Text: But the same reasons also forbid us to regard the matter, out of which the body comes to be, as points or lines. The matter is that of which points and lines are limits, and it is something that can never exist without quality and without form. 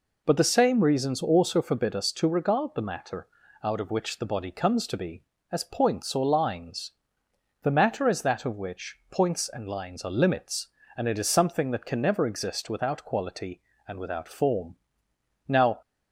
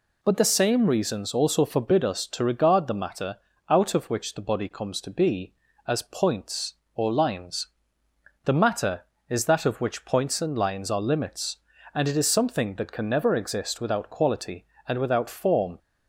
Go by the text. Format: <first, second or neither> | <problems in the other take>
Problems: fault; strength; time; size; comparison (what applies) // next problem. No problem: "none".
second | goes on to say "Now"; slight; from 15.4 s on; 0.34 s long